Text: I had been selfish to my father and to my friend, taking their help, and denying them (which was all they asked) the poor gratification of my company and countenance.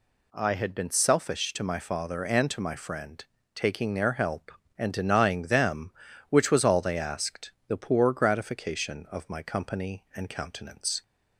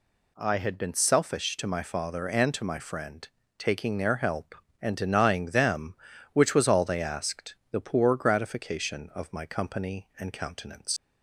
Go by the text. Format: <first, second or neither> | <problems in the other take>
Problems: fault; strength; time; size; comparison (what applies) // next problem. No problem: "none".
first | leaves "countenance" unfinished; at 10.9 s; 90 ms